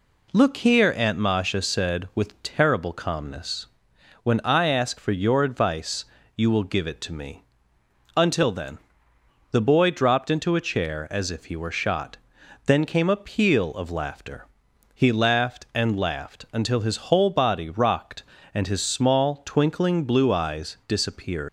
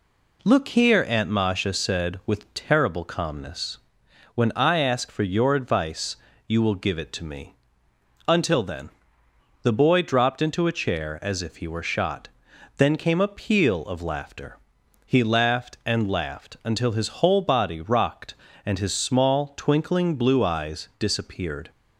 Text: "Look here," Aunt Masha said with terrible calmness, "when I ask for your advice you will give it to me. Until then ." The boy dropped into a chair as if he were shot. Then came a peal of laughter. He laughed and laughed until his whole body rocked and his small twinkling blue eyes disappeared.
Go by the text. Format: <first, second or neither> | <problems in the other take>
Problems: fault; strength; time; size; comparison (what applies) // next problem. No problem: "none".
second | pauses between "advice" and "you"; slight; at 6.0 s; 0.30 s long; slight in the second // leaves "disappeared" unfinished; at 21.4 s; 105 ms